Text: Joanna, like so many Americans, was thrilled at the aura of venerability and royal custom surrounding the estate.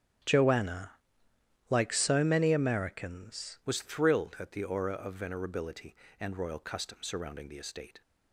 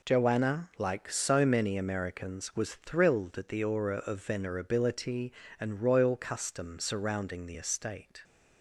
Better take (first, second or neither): second